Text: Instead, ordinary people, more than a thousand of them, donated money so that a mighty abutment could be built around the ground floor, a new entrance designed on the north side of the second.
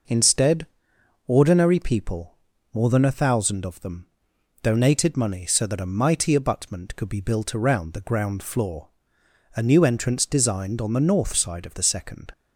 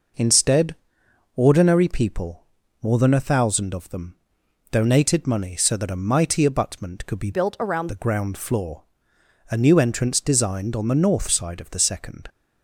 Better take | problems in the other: first | changes voice from "built" to "around"; from 7.3 to 7.8 s; 0.5 s long

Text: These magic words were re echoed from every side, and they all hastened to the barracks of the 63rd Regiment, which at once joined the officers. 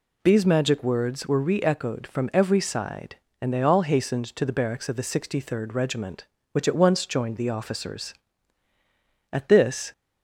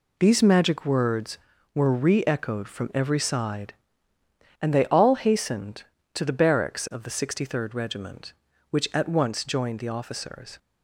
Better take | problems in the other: second | goes on to say "At this"; noticeable; from 9.3 s on; 0.61 s long

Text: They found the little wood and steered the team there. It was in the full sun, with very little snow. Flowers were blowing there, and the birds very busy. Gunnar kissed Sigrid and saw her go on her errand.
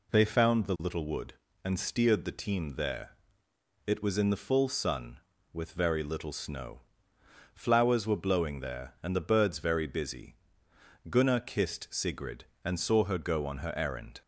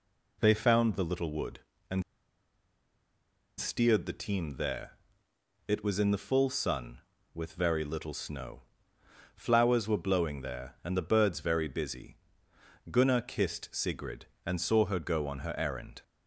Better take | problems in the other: first | pauses between "and" and "steered"; strong; at 2.0 s; 1.5 s long

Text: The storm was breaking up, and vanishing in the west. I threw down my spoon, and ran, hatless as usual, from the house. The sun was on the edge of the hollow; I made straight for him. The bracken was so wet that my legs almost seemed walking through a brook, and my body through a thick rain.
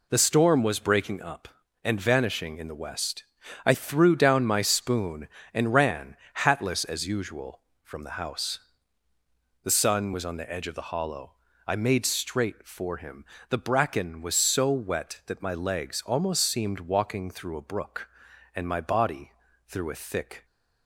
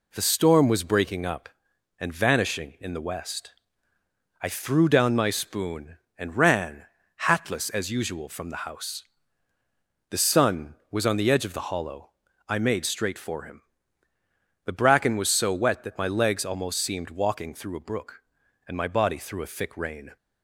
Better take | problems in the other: second | pauses between "body" and "through"; slight; at 19.3 s; 0.34 s long // stops before "rain"; at 20.4 s

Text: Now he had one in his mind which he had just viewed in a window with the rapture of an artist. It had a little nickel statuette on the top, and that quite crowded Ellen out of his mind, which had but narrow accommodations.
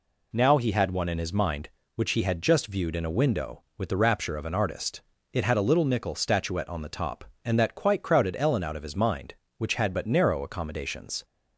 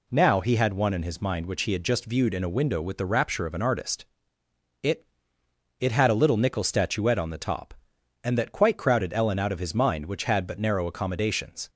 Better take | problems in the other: first | says "It" twice; at 5.8 s

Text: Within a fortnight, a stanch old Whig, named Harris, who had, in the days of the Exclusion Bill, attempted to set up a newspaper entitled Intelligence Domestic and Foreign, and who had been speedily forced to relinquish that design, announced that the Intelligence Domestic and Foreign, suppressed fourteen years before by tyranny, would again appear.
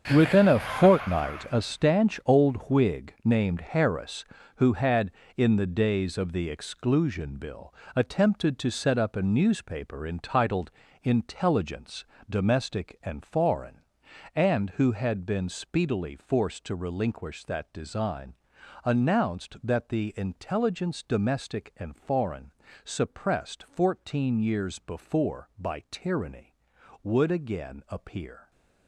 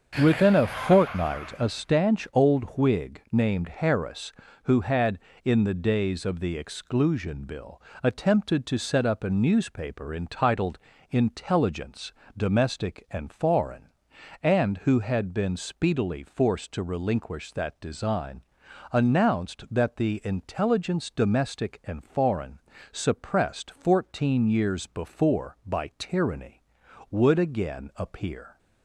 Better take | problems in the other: second | gets quieter; strong; throughout; 13.5 dB // starts louder than the rest; strong; until 1.1 s; 8 dB; also in the second // pauses between "entitled" and "Intelligence"; slight; at 10.7 s; 0.32 s long; slight in the second // pauses between "Intelligence" and "Domestic"; slight; at 12.0 s; 0.26 s long; slight in the second

